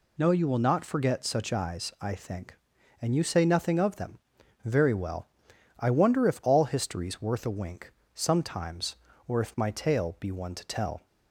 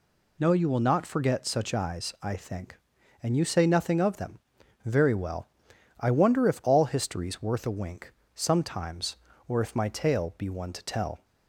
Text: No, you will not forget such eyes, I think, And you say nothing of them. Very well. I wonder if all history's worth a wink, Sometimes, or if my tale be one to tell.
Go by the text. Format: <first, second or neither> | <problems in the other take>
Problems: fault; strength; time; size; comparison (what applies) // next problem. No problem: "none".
neither | none